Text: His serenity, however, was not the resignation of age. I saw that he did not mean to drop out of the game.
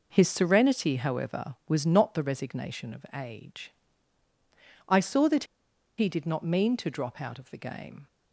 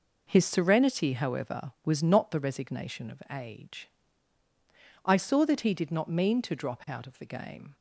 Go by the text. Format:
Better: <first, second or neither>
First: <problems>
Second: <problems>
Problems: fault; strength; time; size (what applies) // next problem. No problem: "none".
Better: second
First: pauses between "that" and "he"; noticeable; at 5.4 s; 0.52 s long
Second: none